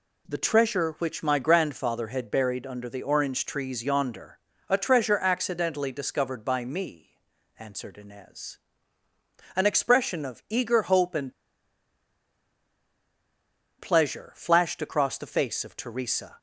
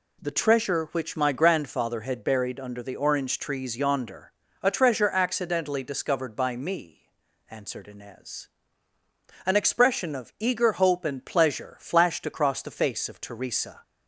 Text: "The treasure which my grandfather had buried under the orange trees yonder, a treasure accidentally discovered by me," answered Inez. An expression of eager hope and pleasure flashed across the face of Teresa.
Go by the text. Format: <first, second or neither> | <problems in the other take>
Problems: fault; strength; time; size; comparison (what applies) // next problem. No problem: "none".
second | pauses between "and" and "pleasure"; strong; at 11.3 s; 2.4 s long